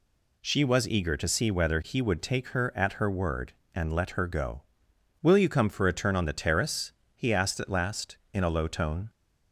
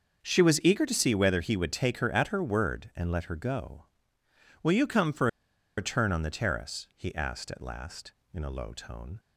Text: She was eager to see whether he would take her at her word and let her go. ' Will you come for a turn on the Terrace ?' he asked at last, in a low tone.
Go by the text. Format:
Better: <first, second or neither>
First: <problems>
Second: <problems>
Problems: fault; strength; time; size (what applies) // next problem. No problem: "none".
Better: first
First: none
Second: starts louder than the rest; until 1.2 s; 6.5 dB // pauses between "for" and "a"; noticeable; at 5.2 s; 0.50 s long